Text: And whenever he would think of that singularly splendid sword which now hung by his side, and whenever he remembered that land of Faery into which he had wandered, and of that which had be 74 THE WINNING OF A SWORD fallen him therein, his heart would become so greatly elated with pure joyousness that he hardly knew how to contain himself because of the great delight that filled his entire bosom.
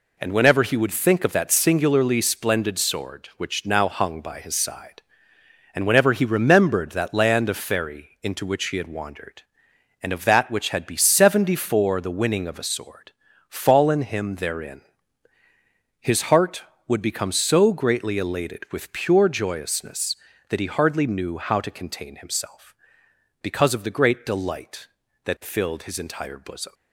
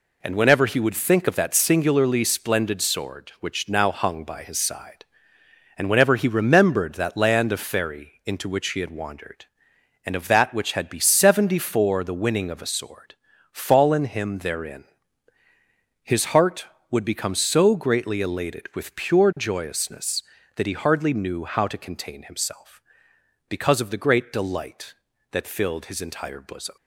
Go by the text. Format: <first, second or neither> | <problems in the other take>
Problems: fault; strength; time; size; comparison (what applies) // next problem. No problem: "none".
neither | pauses between "SWORD" and "fallen"; slight; the same in both